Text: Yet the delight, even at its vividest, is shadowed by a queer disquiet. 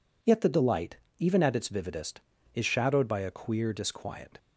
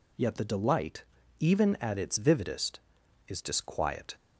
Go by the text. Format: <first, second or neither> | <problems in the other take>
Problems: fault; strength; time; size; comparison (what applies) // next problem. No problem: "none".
first | skips "shadowed by a queer"; at 3.4 s